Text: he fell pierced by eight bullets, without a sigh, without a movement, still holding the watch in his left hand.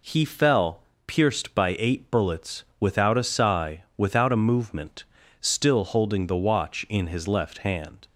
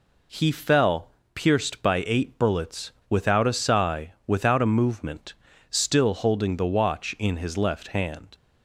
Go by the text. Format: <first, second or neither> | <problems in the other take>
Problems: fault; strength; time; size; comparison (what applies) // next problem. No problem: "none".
neither | pauses between "fell" and "pierced"; slight; the same in both